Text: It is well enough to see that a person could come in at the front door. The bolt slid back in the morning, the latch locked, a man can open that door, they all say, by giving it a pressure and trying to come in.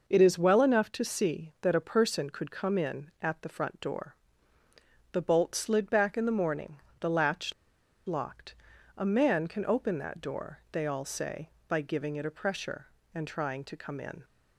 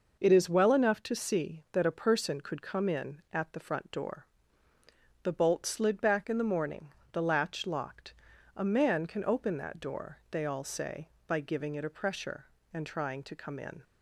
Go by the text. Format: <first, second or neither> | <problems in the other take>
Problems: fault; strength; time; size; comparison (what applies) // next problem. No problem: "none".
second | pauses between "latch" and "locked"; noticeable; at 7.5 s; 0.53 s long